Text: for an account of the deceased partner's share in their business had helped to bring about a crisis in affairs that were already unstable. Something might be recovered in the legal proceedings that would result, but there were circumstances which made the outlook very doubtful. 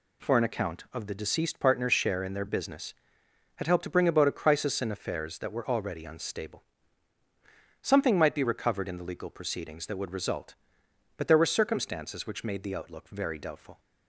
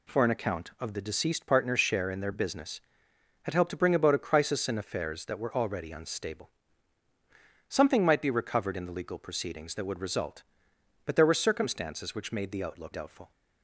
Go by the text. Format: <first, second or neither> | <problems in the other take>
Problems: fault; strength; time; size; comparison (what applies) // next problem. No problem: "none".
first | skips "very"; at 12.9 s